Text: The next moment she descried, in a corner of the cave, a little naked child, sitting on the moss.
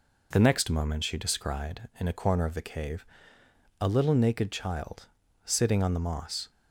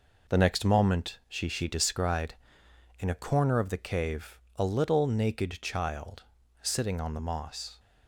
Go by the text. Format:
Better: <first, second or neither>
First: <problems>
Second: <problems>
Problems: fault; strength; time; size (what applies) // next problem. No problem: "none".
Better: first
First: none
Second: says "she" twice; at 1.4 s